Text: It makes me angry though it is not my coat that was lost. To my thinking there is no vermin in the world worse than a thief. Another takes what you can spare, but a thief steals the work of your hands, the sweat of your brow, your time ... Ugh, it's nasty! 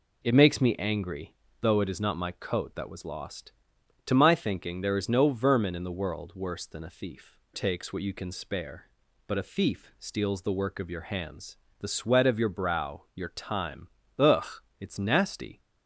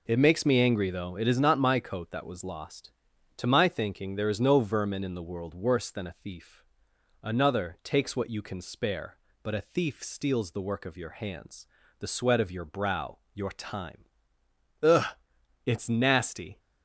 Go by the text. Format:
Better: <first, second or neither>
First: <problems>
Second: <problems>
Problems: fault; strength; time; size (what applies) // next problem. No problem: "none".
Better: second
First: pauses between "angry" and "though"; slight; at 1.3 s; 0.28 s long // skips "Another"; at 7.4 s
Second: none